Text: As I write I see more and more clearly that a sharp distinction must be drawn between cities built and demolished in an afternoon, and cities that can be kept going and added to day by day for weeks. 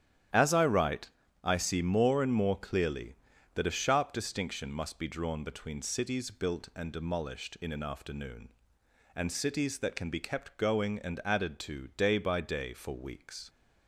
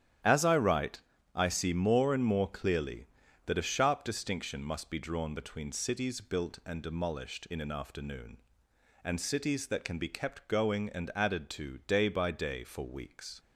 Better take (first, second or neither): neither